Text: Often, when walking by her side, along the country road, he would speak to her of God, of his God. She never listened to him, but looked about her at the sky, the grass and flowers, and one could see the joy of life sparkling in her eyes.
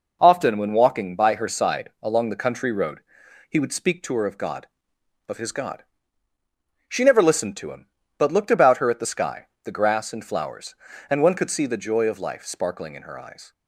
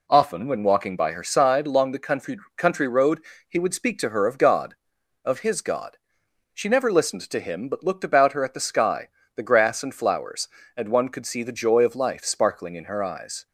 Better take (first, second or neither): first